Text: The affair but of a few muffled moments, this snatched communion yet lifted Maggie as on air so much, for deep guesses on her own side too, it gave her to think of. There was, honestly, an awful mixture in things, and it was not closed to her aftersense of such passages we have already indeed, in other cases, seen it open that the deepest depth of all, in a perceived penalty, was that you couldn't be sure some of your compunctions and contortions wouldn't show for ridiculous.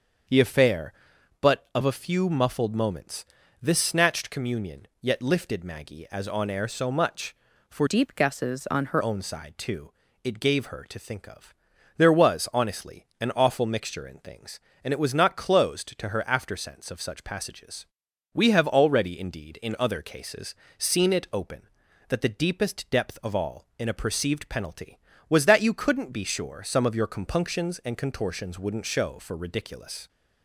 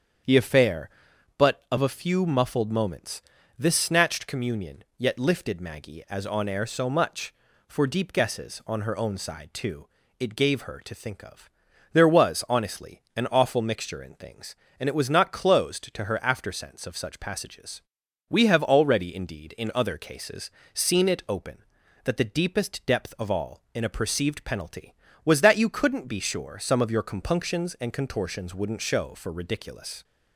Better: second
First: starts louder than the rest; until 1.8 s; 6.5 dB // changes voice from "deep" to "her"; from 7.8 to 9.0 s; 1.2 s long // pauses between "passages" and "we"; noticeable; at 17.8 s; 0.46 s long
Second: starts louder than the rest; strong; until 1.8 s; 7.5 dB // pauses between "passages" and "we"; noticeable; at 17.8 s; 0.46 s long

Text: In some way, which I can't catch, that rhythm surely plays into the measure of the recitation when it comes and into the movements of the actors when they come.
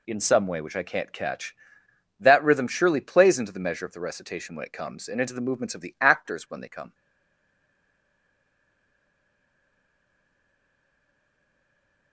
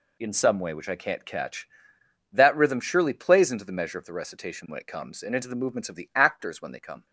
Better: second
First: stays silent after the last word; strong; from 6.9 s on; 5.2 s long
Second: none

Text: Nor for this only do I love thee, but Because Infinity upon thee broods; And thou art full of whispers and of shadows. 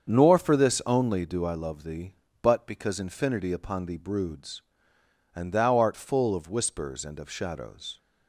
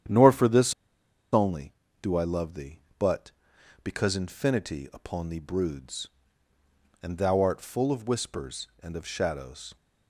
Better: first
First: starts louder than the rest; strong; until 1.1 s; 7 dB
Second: starts louder than the rest; strong; until 1.6 s; 9.5 dB // pauses between "this" and "only"; noticeable; at 0.7 s; 0.60 s long

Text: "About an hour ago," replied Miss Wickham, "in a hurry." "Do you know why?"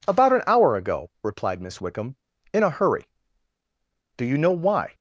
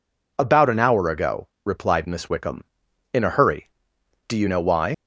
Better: first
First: none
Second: leaves "why" unfinished; at 4.9 s; 75 ms

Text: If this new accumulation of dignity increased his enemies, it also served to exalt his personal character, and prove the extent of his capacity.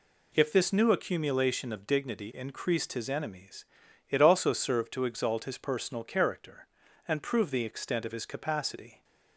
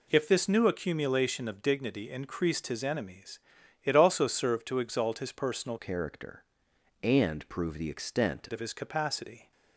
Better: first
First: none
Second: changes voice from "character" to "extent"; from 5.7 to 8.4 s; 2.7 s long

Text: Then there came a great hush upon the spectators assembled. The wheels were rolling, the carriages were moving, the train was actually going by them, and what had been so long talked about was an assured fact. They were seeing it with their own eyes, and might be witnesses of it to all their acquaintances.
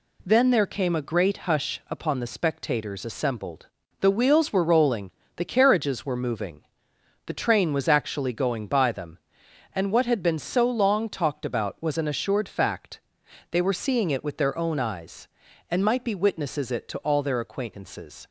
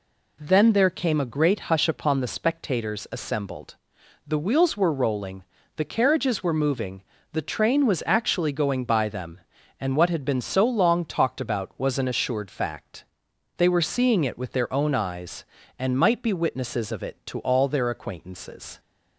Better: second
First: skips "of"; at 16.7 s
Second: none

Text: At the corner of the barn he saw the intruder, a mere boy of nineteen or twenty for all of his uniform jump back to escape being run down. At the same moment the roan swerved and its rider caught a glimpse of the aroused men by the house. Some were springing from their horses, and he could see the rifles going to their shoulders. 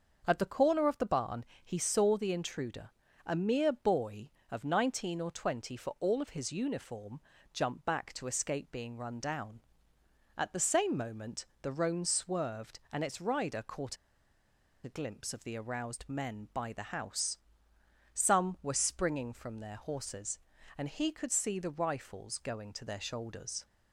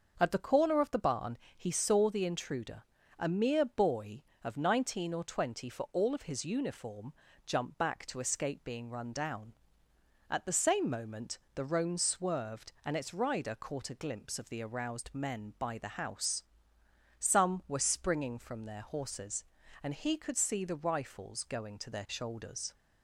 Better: second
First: starts louder than the rest; until 1.2 s; 6.5 dB // pauses between "barn" and "he"; slight; at 1.4 s; 0.20 s long // pauses between "uniform" and "jump"; slight; at 7.1 s; 0.32 s long // pauses between "moment" and "the"; slight; at 11.4 s; 0.16 s long // pauses between "caught" and "a"; noticeable; at 13.9 s; 0.88 s long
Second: starts louder than the rest; until 1.1 s; 6.5 dB // pauses between "barn" and "he"; slight; at 1.3 s; 0.20 s long // pauses between "uniform" and "jump"; slight; at 7.1 s; 0.32 s long // pauses between "moment" and "the"; slight; at 11.3 s; 0.16 s long

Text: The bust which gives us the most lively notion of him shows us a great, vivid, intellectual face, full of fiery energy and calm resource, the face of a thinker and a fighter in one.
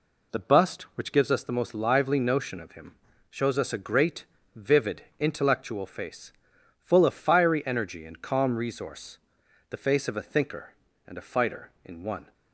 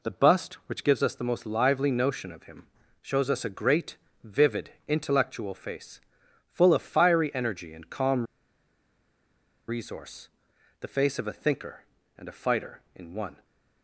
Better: first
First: pauses between "him" and "shows"; slight; at 2.9 s; 0.36 s long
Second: pauses between "him" and "shows"; slight; at 2.6 s; 0.36 s long // pauses between "calm" and "resource"; strong; at 8.2 s; 1.4 s long

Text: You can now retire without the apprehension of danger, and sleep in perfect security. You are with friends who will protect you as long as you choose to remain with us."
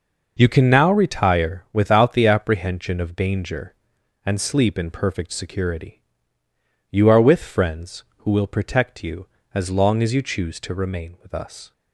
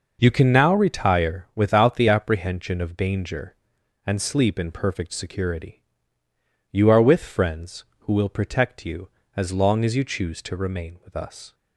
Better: neither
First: none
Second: none

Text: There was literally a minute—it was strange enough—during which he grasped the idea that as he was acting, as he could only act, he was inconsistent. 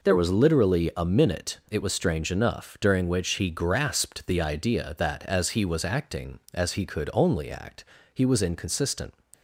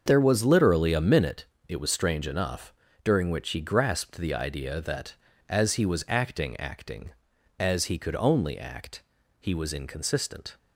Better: first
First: none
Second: starts louder than the rest; until 1.0 s; 6.5 dB // says "acting" twice; at 6.6 s

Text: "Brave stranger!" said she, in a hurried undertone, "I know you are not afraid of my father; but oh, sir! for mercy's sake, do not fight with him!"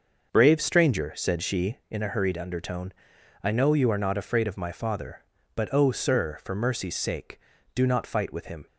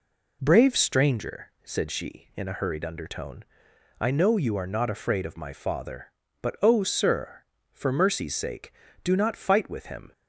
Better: second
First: starts louder than the rest; until 2.0 s; 6 dB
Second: none

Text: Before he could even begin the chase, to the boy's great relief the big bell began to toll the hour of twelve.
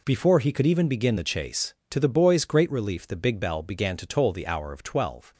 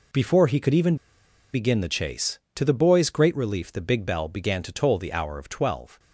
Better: first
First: none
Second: pauses between "even" and "begin"; noticeable; at 0.9 s; 0.58 s long

